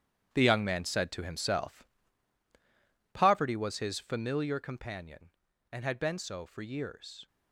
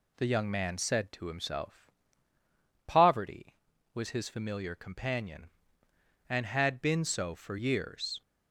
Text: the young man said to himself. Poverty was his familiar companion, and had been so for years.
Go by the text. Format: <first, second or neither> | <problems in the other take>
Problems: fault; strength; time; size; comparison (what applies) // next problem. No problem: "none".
second | gets quieter; strong; throughout; 11.5 dB